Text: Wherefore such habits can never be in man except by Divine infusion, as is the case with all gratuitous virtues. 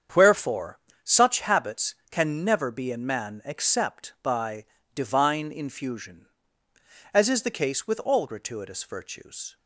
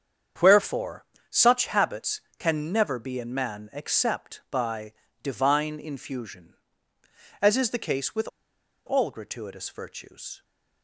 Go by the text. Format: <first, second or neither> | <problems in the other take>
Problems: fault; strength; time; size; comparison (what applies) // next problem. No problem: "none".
first | starts louder than the rest; strong; until 1.6 s; 7.5 dB; strong in the first // pauses between "Wherefore" and "such"; slight; at 1.0 s; 0.26 s long; slight in the first // pauses between "by" and "Divine"; slight; at 4.9 s; 0.30 s long; slight in the first // pauses between "with" and "all"; noticeable; at 8.2 s; 0.57 s long